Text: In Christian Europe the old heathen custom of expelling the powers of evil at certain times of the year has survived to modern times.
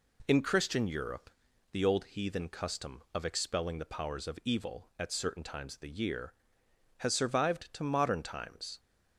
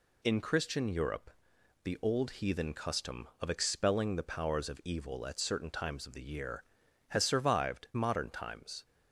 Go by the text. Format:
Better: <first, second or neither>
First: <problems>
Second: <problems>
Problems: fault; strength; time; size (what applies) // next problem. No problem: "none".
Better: first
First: pauses between "Europe" and "the"; at 1.3 s; 0.40 s long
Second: pauses between "Europe" and "the"; noticeable; at 1.3 s; 0.50 s long // skips "to"; at 7.9 s